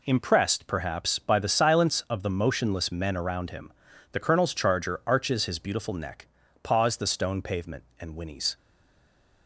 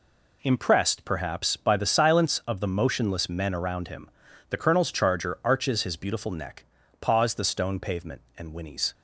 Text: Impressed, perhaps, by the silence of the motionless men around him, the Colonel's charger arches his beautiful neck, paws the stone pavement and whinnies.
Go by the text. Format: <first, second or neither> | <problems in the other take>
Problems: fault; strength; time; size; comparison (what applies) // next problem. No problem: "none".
second | stays silent after the last word; slight; from 8.5 s on; 0.9 s long